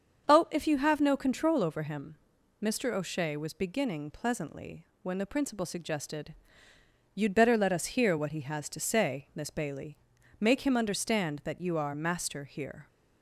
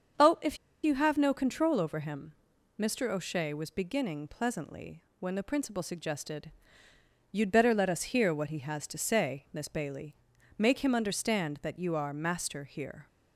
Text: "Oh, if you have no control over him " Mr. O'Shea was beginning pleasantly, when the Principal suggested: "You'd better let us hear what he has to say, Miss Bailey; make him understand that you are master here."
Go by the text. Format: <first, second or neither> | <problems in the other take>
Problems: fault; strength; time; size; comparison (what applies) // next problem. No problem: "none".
first | starts louder than the rest; until 1.5 s; 7 dB; also in the first // pauses between "if" and "you"; slight; at 0.5 s; 0.26 s long